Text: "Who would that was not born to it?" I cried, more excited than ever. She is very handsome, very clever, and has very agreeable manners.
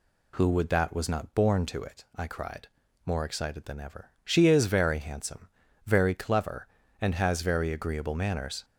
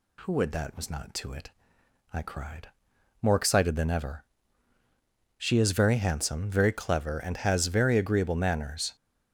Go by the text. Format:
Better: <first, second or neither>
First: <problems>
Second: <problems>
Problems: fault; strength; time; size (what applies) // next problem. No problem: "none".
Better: first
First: none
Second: skips "born"; at 1.1 s